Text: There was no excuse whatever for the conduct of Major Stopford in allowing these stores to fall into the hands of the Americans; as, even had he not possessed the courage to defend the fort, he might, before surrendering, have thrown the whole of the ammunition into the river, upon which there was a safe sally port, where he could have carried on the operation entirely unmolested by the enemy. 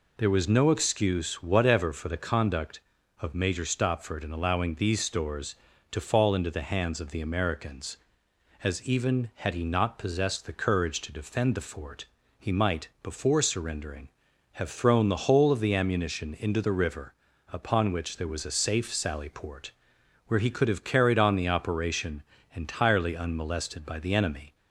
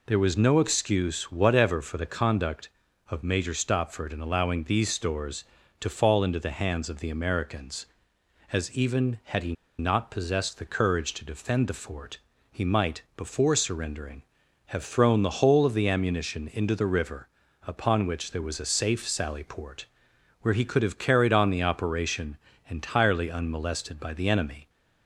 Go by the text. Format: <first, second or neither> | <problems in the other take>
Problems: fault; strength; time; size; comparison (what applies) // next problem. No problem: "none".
first | pauses between "he" and "not"; slight; at 9.5 s; 0.25 s long // pauses between "operation" and "entirely"; slight; at 22.3 s; 0.30 s long; slight in the first